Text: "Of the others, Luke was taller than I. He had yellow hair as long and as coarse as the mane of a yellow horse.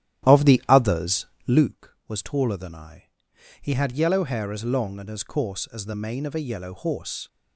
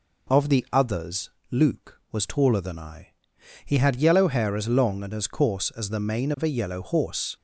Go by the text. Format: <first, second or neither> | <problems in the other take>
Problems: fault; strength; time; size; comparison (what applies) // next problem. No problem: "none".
second | starts louder than the rest; strong; until 1.7 s; 12 dB